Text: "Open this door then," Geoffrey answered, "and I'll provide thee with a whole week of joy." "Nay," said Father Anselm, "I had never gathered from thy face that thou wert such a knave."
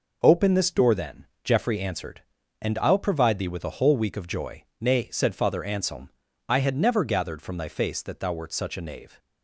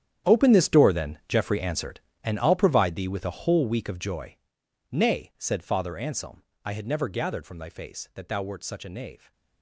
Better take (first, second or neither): first